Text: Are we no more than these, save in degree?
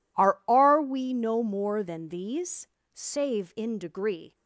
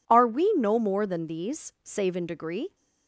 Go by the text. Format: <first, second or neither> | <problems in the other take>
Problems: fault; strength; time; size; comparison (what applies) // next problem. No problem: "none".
second | says "Are" twice; at 0.4 s